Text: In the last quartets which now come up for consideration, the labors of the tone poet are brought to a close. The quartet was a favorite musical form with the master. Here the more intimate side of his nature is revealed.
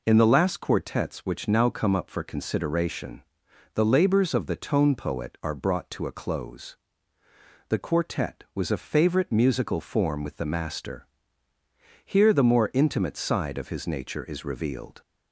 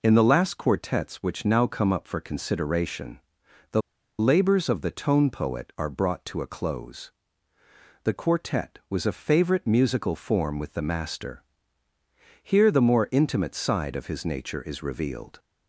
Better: first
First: none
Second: pauses between "the" and "labors"; at 3.8 s; 0.37 s long

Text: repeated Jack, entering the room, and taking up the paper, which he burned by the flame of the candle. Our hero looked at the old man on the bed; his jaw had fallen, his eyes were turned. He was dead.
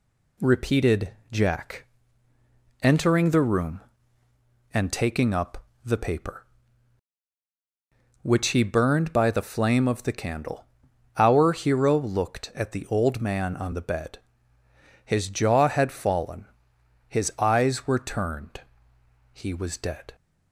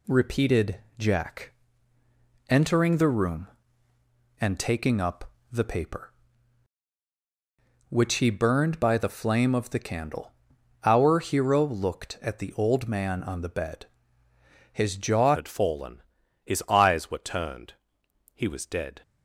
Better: first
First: pauses between "repeated" and "Jack"; slight; at 1.1 s; 0.22 s long // pauses between "up" and "the"; slight; at 5.6 s; 0.20 s long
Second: pauses between "repeated" and "Jack"; slight; at 0.7 s; 0.22 s long // pauses between "up" and "the"; slight; at 5.3 s; 0.20 s long // changes voice at "had"; from 15.3 s on; 3.7 s long

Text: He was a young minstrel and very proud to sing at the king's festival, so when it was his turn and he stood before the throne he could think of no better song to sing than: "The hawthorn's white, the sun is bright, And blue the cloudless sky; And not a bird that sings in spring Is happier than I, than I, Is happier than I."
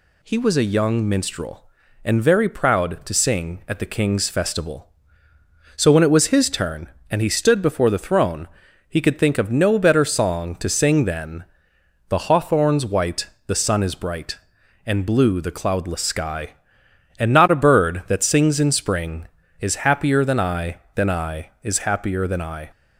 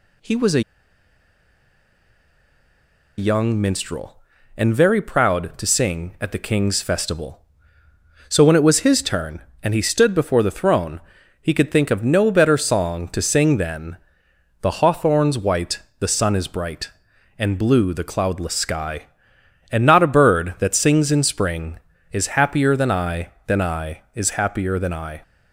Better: first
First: pauses between "throne" and "he"; at 8.4 s; 0.42 s long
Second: pauses between "a" and "young"; strong; at 0.6 s; 2.5 s long // pauses between "throne" and "he"; at 10.9 s; 0.42 s long

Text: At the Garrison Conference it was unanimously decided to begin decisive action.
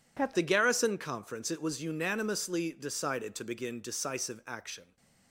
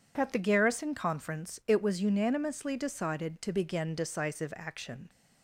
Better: second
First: changes voice at "the"; from 0.3 s on; 4.6 s long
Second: none

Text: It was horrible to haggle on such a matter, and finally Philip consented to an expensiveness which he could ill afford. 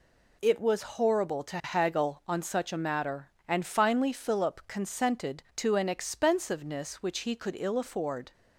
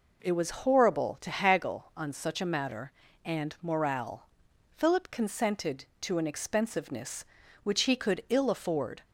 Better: first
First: none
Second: says "morale" for "finally"; at 3.6 s

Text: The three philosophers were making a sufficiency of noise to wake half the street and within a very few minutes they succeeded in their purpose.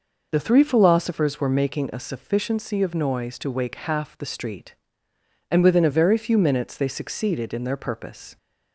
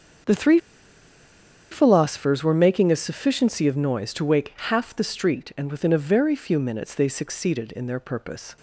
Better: first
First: none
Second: starts louder than the rest; strong; until 2.4 s; 7 dB // pauses between "three" and "philosophers"; at 0.5 s; 1.1 s long

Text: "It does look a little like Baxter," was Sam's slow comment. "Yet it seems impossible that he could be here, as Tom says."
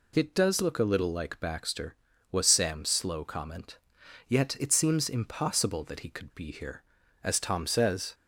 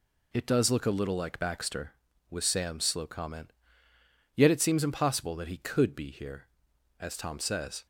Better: neither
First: none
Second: none

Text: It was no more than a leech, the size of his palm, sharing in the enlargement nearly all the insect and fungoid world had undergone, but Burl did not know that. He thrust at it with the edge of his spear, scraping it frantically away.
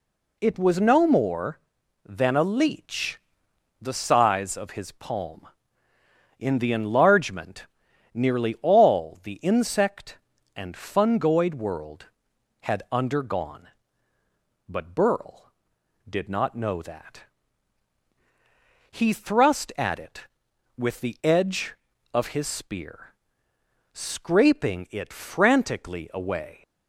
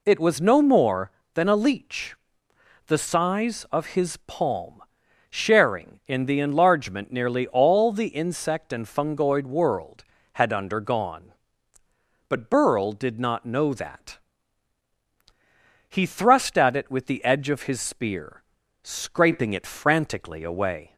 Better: second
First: skips "sharing"; at 5.9 s // pauses between "enlargement" and "nearly"; noticeable; at 7.6 s; 0.46 s long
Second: none

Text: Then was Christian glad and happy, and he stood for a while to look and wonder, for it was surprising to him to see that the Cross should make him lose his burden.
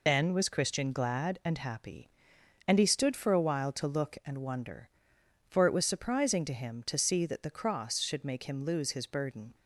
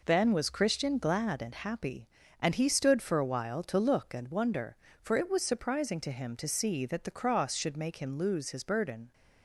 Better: second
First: loses the start of "Then"; at 0.0 s; 50 ms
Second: none

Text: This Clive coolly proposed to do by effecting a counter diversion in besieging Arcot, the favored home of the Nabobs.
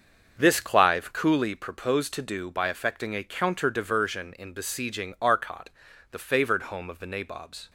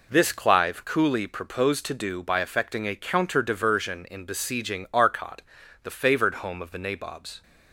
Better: second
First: starts louder than the rest; until 1.6 s; 6.5 dB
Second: none

